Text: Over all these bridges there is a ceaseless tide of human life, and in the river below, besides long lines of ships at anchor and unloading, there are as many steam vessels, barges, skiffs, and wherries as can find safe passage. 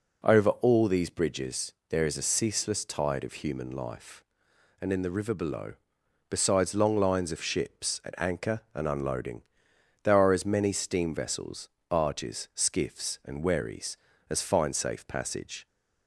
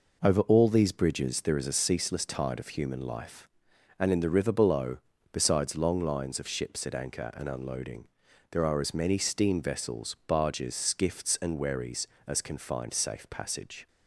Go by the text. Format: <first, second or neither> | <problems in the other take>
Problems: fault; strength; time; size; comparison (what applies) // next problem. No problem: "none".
second | pauses between "bridges" and "there"; slight; at 1.7 s; 0.18 s long // skips "can"; at 14.4 s